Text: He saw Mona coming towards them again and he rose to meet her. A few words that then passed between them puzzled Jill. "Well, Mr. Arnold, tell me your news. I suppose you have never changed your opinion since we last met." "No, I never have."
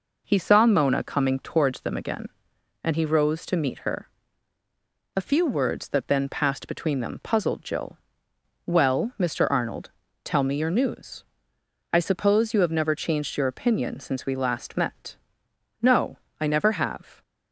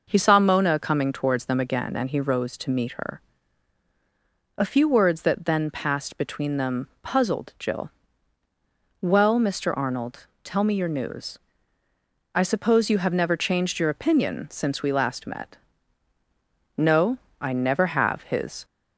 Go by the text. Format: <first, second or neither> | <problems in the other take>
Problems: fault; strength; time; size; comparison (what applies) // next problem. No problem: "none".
first | goes on to say "His"; slight; from 18.2 s on; 0.42 s long